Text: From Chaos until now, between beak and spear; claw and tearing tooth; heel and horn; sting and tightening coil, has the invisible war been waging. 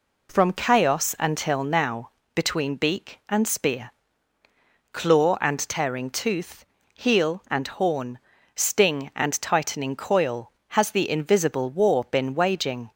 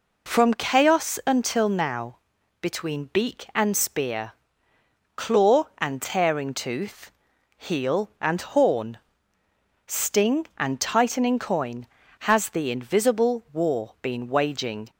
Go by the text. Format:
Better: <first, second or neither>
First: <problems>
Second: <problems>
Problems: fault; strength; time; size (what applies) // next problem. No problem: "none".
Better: first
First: none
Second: says "coin" for "coil"; at 11.3 s